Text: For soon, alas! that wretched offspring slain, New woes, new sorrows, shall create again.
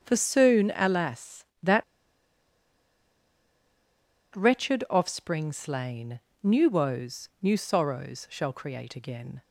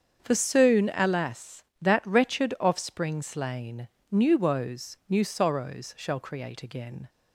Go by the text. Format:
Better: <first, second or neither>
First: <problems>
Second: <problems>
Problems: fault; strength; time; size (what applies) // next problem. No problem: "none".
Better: second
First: starts louder than the rest; strong; until 1.0 s; 7 dB // pauses between "that" and "wretched"; strong; at 1.8 s; 2.5 s long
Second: starts louder than the rest; strong; until 1.2 s; 7 dB